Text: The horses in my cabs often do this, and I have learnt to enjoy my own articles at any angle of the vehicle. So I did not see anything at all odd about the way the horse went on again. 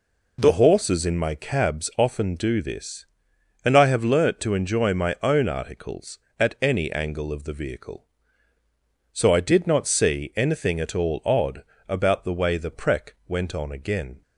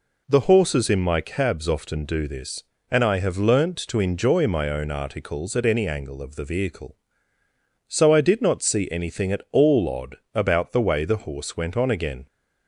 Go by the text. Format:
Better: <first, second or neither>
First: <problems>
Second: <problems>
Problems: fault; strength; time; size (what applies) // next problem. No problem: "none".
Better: second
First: pauses between "odd" and "about"; slight; at 11.6 s; 0.26 s long // says "prec" for "horse"; at 12.7 s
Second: pauses between "odd" and "about"; slight; at 10.1 s; 0.18 s long